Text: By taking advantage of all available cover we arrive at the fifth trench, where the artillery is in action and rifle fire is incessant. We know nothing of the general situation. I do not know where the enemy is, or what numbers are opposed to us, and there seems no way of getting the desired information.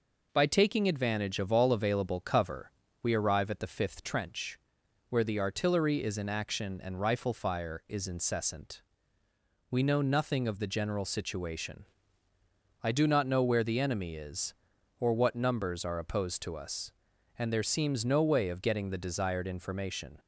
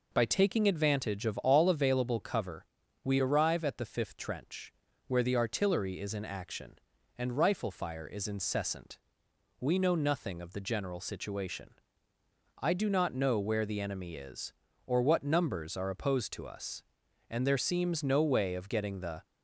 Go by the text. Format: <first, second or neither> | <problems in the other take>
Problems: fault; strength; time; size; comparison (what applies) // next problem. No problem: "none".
first | pauses between "cover" and "we"; slight; at 2.6 s; 0.36 s long; slight in the first // stops before "desired information"; at 19.2 s